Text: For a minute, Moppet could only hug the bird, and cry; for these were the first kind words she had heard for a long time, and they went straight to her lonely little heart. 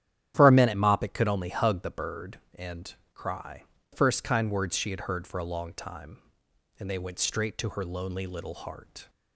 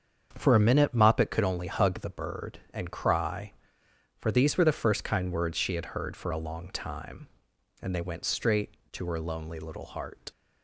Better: second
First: starts louder than the rest; strong; until 1.3 s; 10.5 dB // pauses between "and" and "cry"; slight; at 2.9 s; 0.20 s long // skips "for these were the"; at 3.7 s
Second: starts louder than the rest; strong; until 1.3 s; 7 dB

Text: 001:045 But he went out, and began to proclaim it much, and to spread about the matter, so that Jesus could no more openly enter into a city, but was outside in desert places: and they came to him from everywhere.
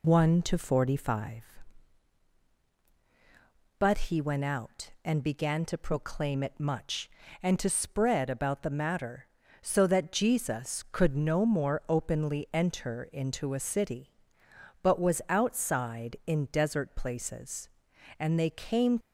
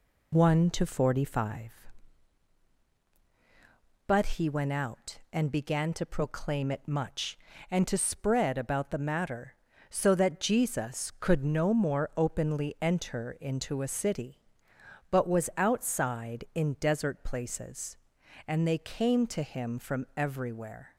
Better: second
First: stops before "to him from everywhere"; at 19.0 s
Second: none

